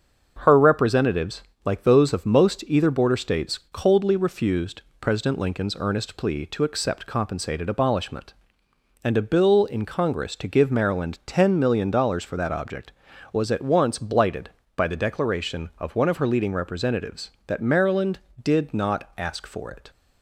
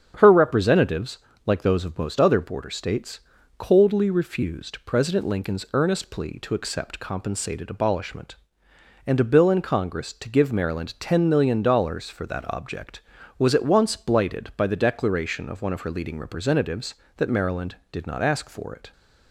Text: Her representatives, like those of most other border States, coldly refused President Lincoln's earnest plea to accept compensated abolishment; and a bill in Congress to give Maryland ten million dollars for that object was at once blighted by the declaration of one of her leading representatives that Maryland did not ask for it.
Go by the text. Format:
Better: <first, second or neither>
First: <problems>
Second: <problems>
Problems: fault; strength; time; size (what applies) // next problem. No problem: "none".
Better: second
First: starts louder than the rest; until 1.4 s; 6.5 dB // says "either" for "other"; at 2.6 s // pauses between "refused" and "President"; slight; at 4.8 s; 0.20 s long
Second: starts louder than the rest; strong; until 1.4 s; 8 dB